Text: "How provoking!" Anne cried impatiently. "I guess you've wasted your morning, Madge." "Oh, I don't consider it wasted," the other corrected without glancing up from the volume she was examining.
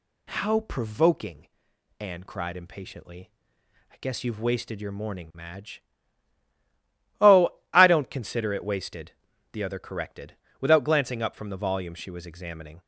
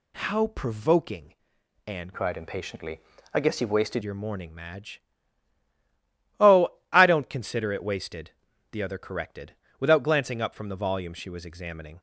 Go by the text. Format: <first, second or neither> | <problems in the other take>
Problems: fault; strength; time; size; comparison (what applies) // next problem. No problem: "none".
first | changes voice from "cried" to "wasted"; from 2.1 to 4.0 s; 1.9 s long // pauses between "corrected" and "without"; slight; at 9.5 s; 0.20 s long; slight in the first